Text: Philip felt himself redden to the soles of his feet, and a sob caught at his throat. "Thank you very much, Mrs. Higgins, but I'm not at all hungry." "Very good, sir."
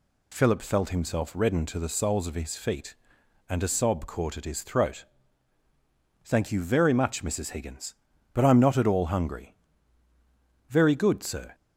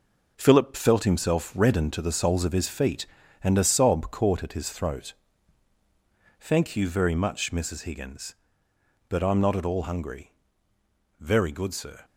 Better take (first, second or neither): first